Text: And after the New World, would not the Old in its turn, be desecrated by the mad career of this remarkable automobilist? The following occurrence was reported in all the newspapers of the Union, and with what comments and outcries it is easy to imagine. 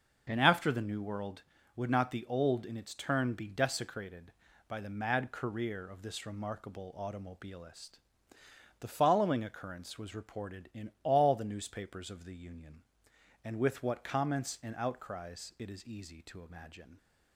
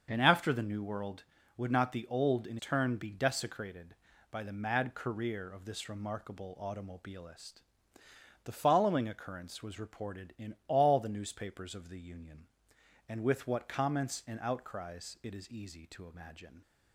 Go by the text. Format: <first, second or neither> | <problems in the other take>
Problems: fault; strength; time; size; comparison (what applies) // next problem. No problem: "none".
first | starts louder than the rest; until 1.1 s; 6.5 dB; noticeable in the first // skips "its"; at 2.5 s